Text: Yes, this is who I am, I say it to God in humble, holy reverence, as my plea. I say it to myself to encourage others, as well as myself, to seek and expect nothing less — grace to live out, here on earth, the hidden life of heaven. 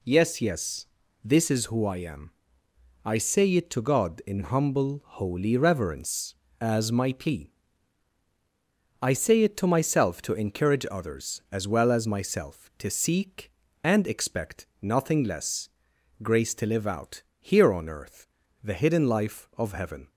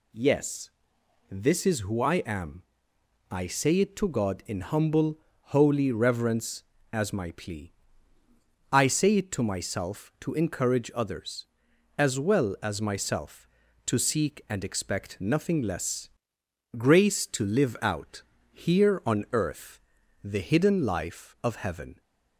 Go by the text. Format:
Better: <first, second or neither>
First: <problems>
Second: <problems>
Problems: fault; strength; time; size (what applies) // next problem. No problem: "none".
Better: second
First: says "Yes" twice; at 0.4 s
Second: none